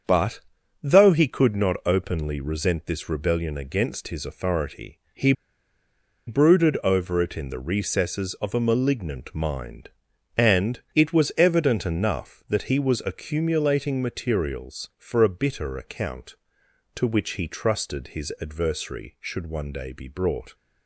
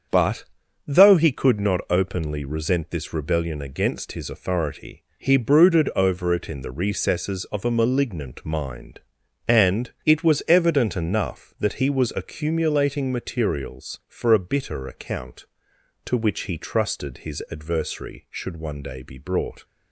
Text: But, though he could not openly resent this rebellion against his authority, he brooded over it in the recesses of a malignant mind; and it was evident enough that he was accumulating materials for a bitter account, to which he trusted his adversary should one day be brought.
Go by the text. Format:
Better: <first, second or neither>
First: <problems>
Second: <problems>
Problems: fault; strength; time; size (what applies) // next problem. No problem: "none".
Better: second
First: starts louder than the rest; strong; until 1.4 s; 7.5 dB // pauses between "he" and "brooded"; noticeable; at 5.3 s; 0.95 s long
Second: starts louder than the rest; strong; until 1.5 s; 7.5 dB